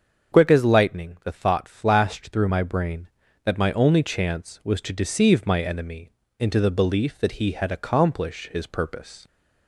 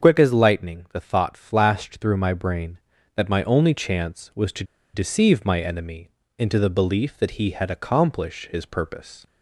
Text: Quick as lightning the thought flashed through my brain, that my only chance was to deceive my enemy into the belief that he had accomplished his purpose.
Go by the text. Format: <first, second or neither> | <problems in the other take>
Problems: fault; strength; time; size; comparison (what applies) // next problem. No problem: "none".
first | starts louder than the rest; until 1.1 s; 6.5 dB; also in the first // pauses between "to" and "deceive"; slight; at 4.6 s; 0.30 s long // pauses between "enemy" and "into"; slight; at 6.0 s; 0.28 s long; slight in the first